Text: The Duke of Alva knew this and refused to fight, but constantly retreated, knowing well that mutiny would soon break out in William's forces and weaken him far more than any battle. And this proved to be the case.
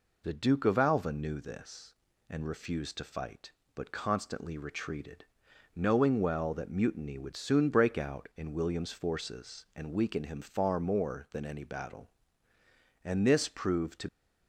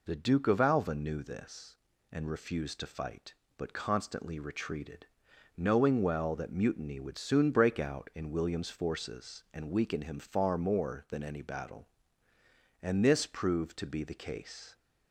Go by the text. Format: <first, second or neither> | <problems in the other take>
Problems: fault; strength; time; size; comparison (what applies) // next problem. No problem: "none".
second | stops before "be the case"; at 14.0 s